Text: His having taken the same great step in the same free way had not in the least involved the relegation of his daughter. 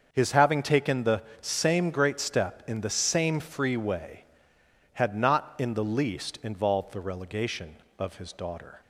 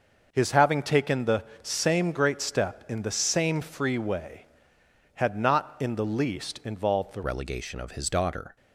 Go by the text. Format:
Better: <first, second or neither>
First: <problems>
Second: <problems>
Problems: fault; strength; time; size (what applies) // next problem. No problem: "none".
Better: first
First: starts louder than the rest; until 1.1 s; 7 dB // pauses between "the" and "same"; slight; at 1.2 s; 0.20 s long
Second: starts louder than the rest; noticeable; until 1.3 s; 6 dB // pauses between "the" and "same"; slight; at 1.4 s; 0.20 s long // changes voice at "relegation"; from 7.2 s on; 1.3 s long